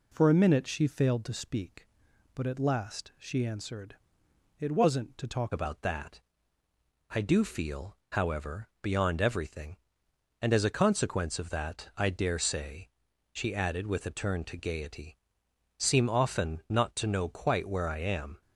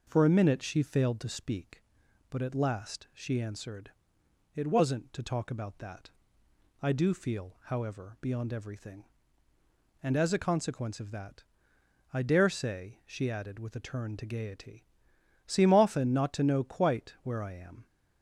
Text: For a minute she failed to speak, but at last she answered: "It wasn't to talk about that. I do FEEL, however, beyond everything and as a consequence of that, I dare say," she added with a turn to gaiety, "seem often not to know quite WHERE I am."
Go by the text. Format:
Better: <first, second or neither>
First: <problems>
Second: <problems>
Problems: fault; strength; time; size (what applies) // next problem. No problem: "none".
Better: second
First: changes voice at "about"; from 5.5 s on; 12.9 s long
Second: none